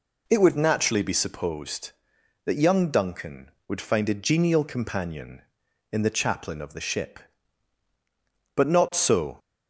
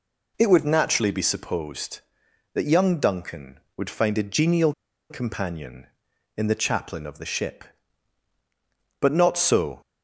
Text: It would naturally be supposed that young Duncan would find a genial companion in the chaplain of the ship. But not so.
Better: first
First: none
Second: pauses between "genial" and "companion"; at 4.7 s; 0.37 s long

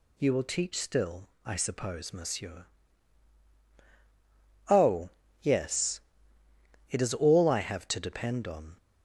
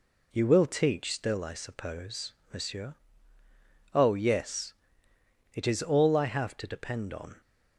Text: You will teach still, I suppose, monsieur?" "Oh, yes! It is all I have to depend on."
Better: neither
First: none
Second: none

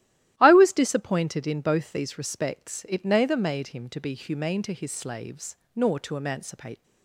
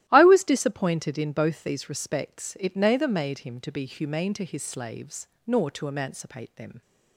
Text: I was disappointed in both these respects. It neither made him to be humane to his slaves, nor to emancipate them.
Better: second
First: starts louder than the rest; strong; until 1.3 s; 14 dB // stops before "them"; at 6.8 s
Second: starts louder than the rest; strong; until 1.0 s; 14 dB

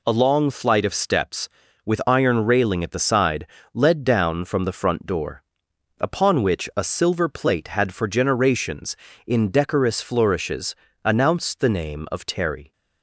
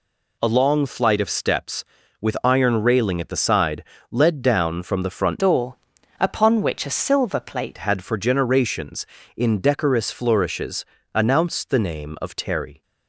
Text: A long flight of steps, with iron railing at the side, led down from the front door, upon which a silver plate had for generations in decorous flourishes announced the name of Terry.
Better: first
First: pauses between "flourishes" and "announced"; slight; at 10.7 s; 0.30 s long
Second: changes voice from "door" to "plate"; from 5.3 to 7.7 s; 2.4 s long // pauses between "flourishes" and "announced"; slight; at 10.8 s; 0.30 s long

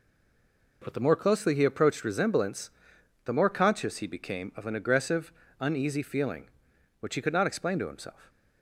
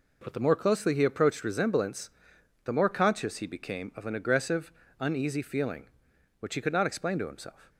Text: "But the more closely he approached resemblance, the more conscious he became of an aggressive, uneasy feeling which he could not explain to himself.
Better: second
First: stays silent before the first word; slight; until 0.8 s; 0.8 s long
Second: none

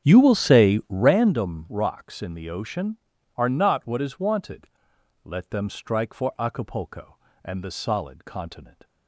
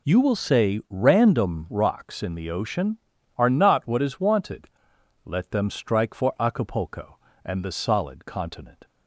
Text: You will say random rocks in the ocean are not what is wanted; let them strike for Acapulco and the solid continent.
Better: second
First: starts louder than the rest; strong; until 1.2 s; 9 dB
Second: none

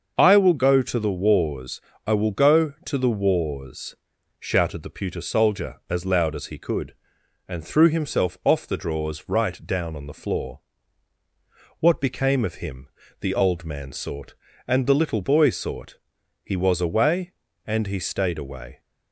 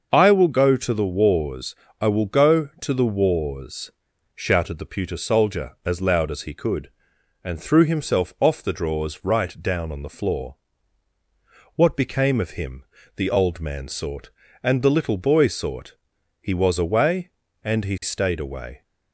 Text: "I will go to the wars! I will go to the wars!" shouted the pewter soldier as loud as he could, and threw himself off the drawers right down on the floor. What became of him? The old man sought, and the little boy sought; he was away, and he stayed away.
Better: neither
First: starts louder than the rest; until 1.1 s; 6.5 dB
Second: starts louder than the rest; until 1.1 s; 6 dB

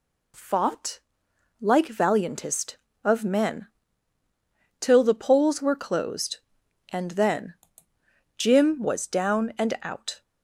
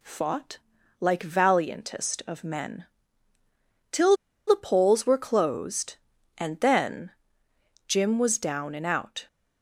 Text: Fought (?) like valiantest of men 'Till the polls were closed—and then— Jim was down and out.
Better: first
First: pauses between "men" and "Till"; at 3.6 s; 1.1 s long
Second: pauses between "men" and "Till"; at 2.8 s; 1.0 s long // pauses between "Till" and "the"; slight; at 4.1 s; 0.31 s long

